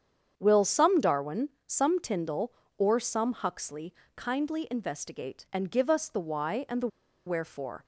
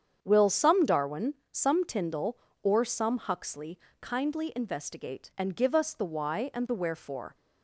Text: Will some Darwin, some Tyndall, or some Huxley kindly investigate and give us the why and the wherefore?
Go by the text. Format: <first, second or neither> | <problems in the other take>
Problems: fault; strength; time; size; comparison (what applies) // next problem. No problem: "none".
second | starts louder than the rest; strong; until 1.3 s; 8 dB; strong in the second // pauses between "Huxley" and "kindly"; slight; at 3.9 s; 0.24 s long; slight in the second // pauses between "the" and "wherefore"; at 6.8 s; 0.39 s long